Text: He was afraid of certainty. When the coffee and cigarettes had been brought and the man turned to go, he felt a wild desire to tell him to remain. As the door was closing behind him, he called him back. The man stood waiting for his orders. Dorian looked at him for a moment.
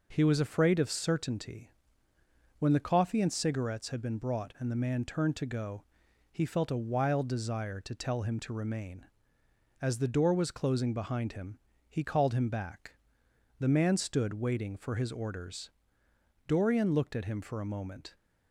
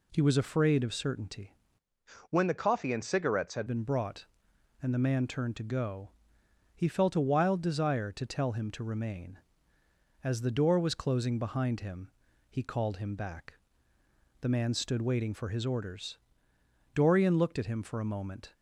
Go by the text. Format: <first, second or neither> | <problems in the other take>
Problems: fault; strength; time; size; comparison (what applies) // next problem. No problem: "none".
first | changes voice from "When" to "had"; from 2.2 to 3.6 s; 1.4 s long